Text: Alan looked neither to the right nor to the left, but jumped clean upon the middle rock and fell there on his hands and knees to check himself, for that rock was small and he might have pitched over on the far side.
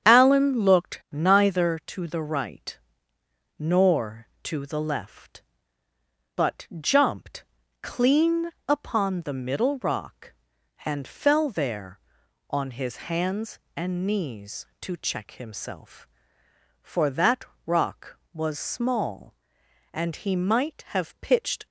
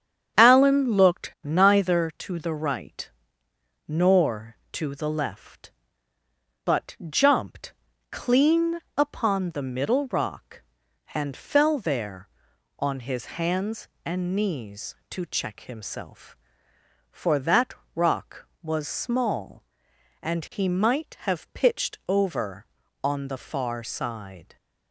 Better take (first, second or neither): second